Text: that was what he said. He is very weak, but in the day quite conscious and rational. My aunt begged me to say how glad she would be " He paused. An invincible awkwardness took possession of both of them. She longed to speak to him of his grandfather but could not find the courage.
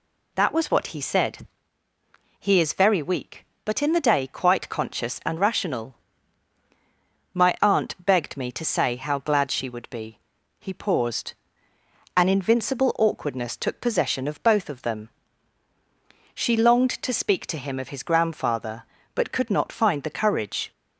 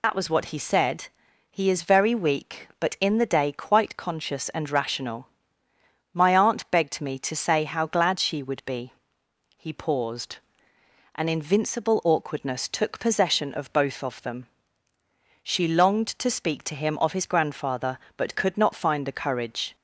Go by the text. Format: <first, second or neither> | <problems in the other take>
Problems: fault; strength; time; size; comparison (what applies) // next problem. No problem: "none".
first | loses the start of "that"; at 0.0 s; 65 ms